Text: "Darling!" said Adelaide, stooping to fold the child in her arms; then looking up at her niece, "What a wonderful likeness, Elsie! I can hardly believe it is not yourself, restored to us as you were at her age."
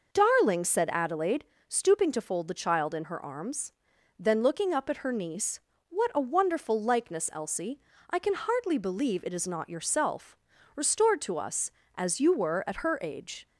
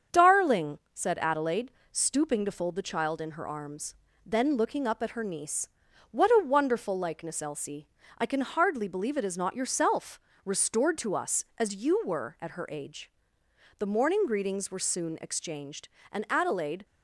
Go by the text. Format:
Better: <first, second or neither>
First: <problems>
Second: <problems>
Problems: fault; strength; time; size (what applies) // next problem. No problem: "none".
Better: first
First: none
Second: starts louder than the rest; strong; until 1.2 s; 7 dB // goes on to say "The morning greetings were soon exchanged and Adelaide"; strong; from 13.7 s on; 3.0 s long